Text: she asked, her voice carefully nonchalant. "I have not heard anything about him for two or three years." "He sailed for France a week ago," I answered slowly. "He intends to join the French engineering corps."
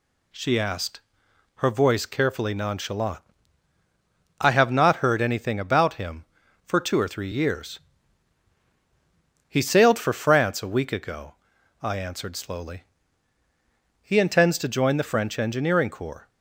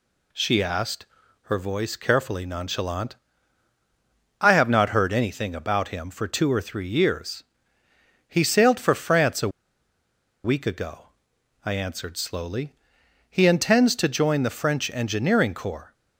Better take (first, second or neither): first